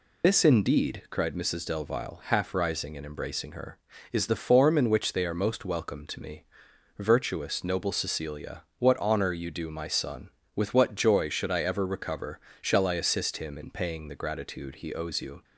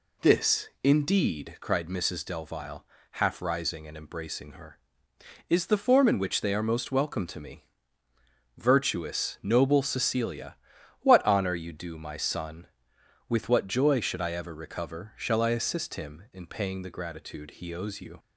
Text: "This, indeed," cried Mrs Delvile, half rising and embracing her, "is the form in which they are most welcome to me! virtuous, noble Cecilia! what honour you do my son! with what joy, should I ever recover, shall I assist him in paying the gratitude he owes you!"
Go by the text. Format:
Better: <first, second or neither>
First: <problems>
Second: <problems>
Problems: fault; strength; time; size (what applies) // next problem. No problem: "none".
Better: second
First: loses the start of "This"; at 0.2 s; 110 ms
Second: none